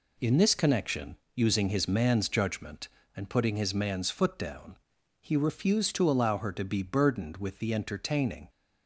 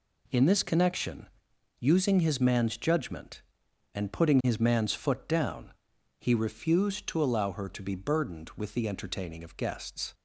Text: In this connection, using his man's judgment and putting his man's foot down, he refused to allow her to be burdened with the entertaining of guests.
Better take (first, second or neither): second